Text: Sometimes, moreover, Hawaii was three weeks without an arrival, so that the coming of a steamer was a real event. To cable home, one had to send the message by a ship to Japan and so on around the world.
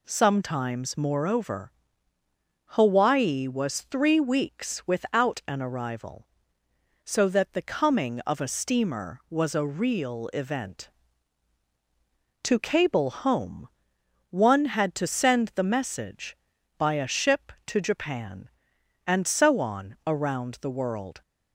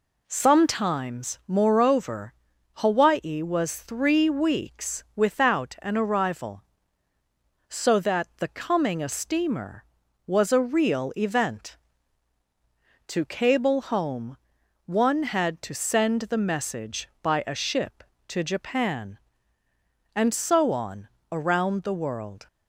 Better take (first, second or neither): first